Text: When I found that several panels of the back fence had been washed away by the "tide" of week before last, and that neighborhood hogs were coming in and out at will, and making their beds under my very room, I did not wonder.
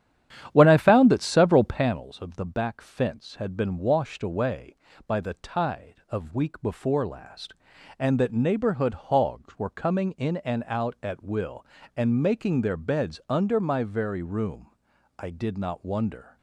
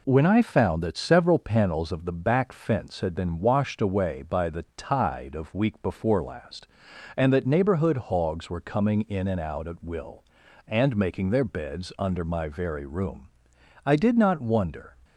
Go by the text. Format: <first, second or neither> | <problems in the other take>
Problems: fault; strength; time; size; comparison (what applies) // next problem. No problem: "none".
second | starts louder than the rest; strong; until 1.9 s; 10 dB